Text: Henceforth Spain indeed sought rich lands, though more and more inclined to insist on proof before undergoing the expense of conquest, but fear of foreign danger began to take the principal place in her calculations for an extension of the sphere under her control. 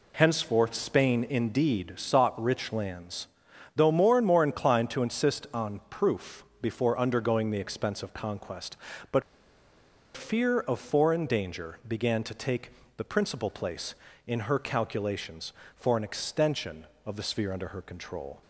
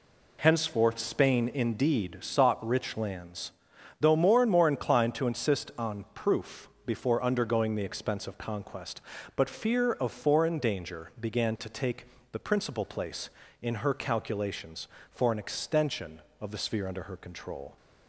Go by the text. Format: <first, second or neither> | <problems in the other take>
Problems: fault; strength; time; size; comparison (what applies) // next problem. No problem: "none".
second | pauses between "proof" and "before"; slight; at 6.4 s; 0.16 s long; slight in the second // pauses between "but" and "fear"; noticeable; at 9.2 s; 0.94 s long // pauses between "take" and "the"; slight; at 12.7 s; 0.26 s long; slight in the second